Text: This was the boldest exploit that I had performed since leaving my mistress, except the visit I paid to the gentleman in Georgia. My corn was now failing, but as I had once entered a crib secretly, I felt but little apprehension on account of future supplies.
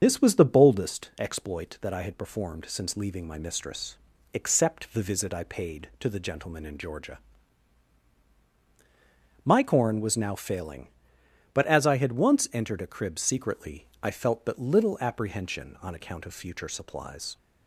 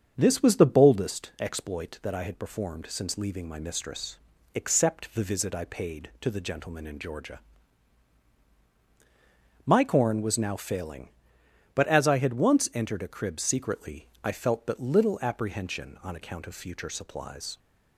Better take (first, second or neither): second